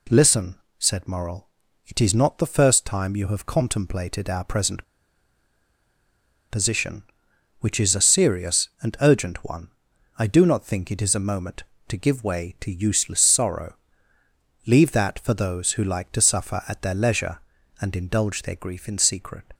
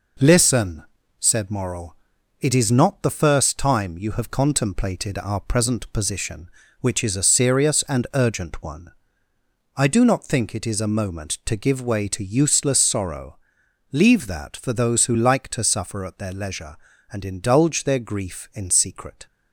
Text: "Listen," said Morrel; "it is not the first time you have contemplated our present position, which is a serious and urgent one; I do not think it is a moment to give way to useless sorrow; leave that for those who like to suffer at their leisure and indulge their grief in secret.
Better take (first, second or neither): second